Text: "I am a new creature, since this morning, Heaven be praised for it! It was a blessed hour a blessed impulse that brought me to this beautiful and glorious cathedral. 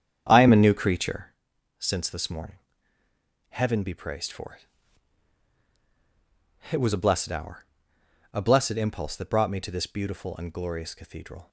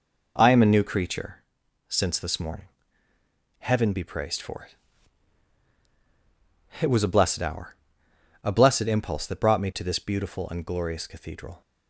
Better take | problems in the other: second | starts louder than the rest; strong; until 1.4 s; 8.5 dB // pauses between "hour" and "a"; noticeable; at 7.6 s; 0.72 s long; noticeable in the second

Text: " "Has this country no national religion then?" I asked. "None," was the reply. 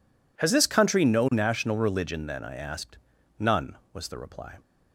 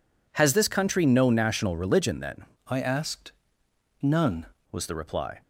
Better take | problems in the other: first | changes voice from "I" to "None"; from 2.6 to 4.4 s; 1.8 s long

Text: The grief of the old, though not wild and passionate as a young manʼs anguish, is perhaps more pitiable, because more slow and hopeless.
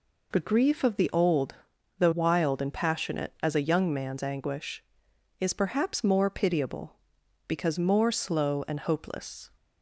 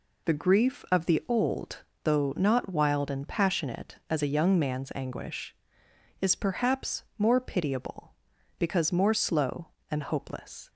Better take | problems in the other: second | skips "not"; at 2.1 s

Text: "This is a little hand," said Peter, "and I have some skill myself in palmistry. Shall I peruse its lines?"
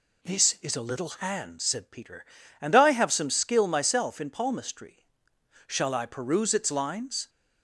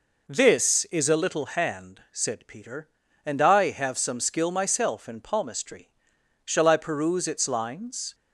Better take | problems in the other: neither | none

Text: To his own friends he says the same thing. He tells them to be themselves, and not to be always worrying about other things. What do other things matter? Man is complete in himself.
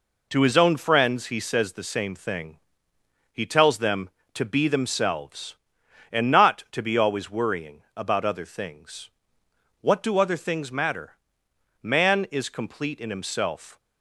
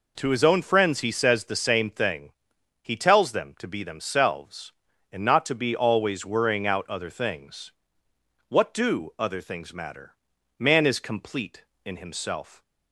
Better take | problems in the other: first | says "out" for "about"; at 6.6 s

